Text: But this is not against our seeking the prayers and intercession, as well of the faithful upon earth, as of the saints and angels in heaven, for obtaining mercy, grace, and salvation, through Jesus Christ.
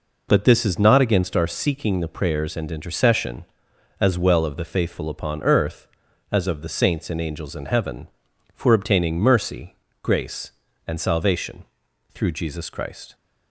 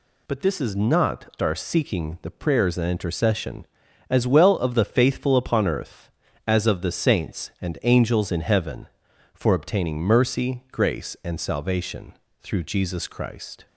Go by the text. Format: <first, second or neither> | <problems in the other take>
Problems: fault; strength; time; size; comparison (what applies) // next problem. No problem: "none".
first | skips "against"; at 1.3 s